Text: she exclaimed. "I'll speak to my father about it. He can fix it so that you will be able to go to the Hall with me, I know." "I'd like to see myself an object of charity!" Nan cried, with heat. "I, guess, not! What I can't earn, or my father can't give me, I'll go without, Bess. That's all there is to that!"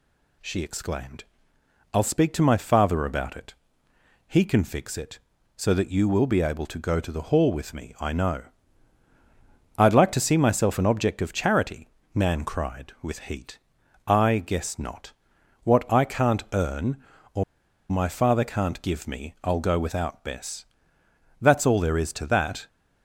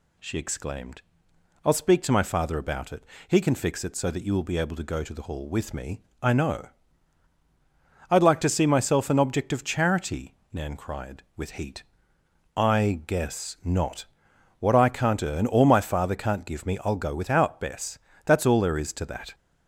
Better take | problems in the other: second | pauses between "or" and "my"; noticeable; at 17.4 s; 0.47 s long

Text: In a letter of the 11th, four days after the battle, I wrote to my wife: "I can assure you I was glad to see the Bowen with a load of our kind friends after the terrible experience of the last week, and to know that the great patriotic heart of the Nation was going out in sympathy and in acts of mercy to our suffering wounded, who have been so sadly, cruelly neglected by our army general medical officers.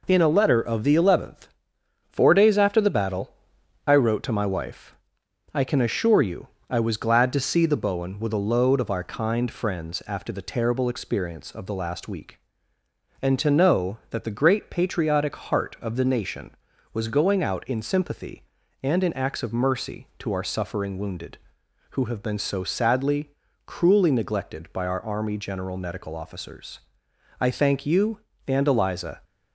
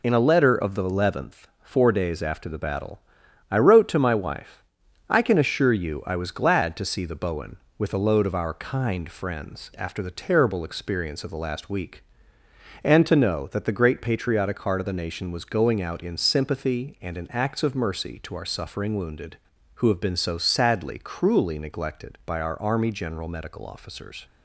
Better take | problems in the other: second | pauses between "you" and "I"; slight; at 6.4 s; 0.22 s long // goes on to say "I thank you and Eliza"; strong; from 27.3 s on; 1.8 s long

